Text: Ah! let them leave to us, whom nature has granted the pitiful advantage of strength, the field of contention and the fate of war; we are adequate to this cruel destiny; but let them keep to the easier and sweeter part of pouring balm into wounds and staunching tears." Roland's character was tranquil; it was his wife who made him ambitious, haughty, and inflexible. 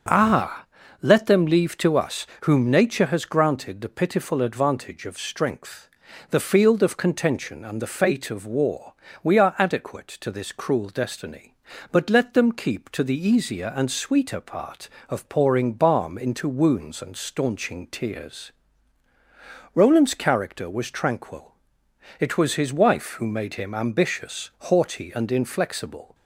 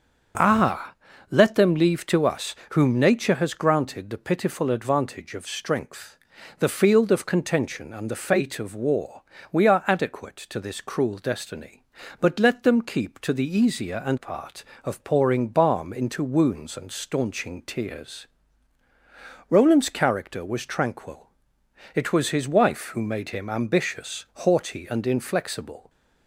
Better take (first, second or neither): first